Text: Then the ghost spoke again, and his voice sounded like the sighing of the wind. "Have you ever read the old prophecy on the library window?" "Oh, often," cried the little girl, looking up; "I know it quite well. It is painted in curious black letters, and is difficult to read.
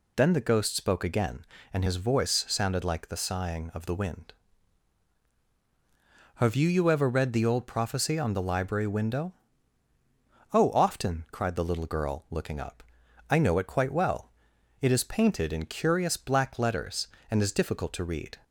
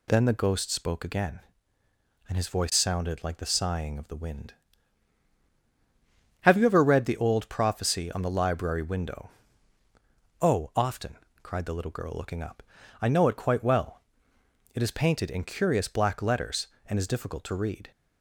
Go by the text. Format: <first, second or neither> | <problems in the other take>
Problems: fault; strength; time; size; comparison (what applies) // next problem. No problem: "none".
second | says "you" twice; at 6.6 s